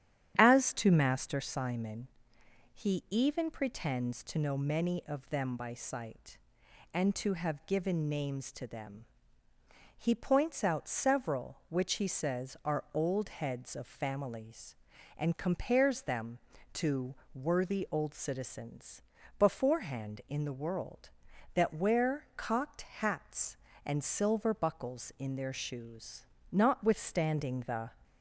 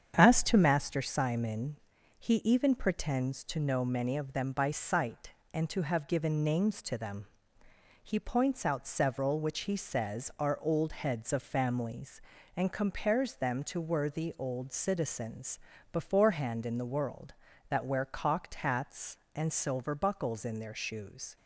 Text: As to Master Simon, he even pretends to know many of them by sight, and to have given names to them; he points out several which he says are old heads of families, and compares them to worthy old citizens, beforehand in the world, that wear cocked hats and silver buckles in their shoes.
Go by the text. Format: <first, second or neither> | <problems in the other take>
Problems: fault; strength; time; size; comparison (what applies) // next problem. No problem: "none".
second | starts louder than the rest; strong; until 1.3 s; 10.5 dB; strong in the second // pauses between "to" and "worthy"; slight; at 17.1 s; 0.20 s long // pauses between "cocked" and "hats"; slight; at 22.8 s; 0.16 s long // goes on to say "Notwithstanding the"; from 26.4 s on; 1.4 s long